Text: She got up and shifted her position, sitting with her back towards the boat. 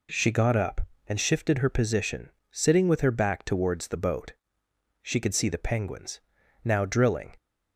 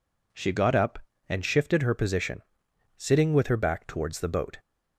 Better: second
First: goes on to say "She could see the penguins now drilling"; strong; from 5.0 s on; 2.3 s long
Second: none

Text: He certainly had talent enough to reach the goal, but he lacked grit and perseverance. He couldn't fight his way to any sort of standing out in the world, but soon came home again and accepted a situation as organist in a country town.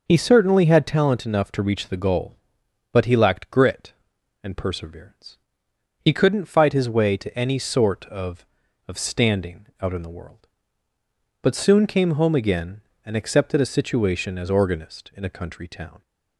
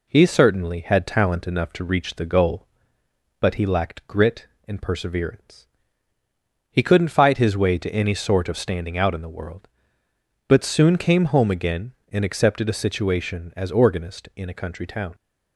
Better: second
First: says "of" twice; at 8.8 s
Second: none

